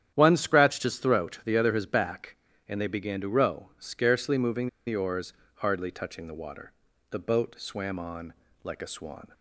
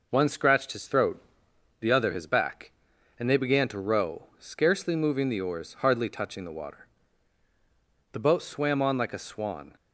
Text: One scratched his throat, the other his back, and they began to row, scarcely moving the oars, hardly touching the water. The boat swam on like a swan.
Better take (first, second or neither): second